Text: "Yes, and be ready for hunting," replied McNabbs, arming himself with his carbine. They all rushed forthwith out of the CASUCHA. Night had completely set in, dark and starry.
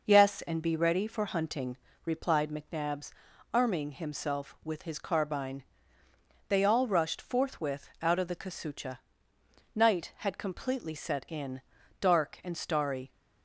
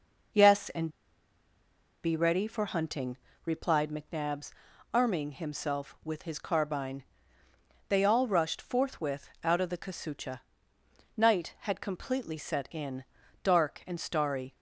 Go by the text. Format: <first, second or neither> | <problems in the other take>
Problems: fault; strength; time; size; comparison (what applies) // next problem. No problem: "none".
first | pauses between "and" and "be"; at 0.8 s; 1.1 s long